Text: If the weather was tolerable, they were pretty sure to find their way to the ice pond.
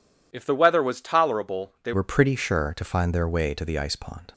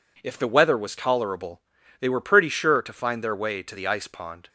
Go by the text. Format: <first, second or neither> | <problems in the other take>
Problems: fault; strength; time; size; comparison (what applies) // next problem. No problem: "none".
second | changes voice at "were"; from 1.9 s on; 2.4 s long